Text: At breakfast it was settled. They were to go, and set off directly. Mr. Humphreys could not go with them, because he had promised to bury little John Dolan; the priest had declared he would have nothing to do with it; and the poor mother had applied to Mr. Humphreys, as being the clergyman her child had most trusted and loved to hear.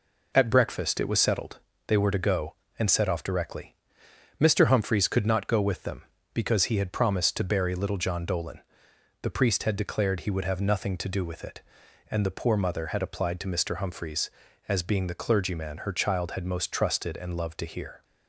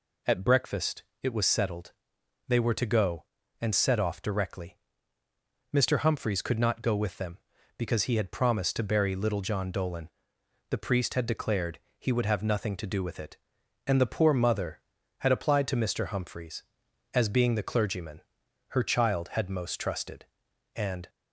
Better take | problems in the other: first | pauses between "breakfast" and "it"; slight; at 1.0 s; 0.20 s long // pauses between "declared" and "he"; slight; at 11.7 s; 0.18 s long // pauses between "clergyman" and "her"; noticeable; at 18.2 s; 0.48 s long // stops before "loved to hear"; at 21.0 s

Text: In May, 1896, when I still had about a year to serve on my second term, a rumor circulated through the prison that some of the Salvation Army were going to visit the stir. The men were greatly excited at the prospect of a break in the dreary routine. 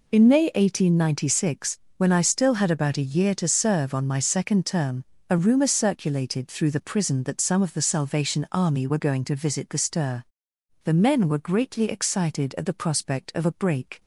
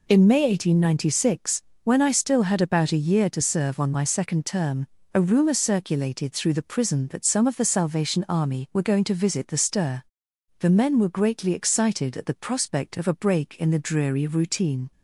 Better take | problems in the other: second | stops before "in the dreary routine"; at 13.9 s

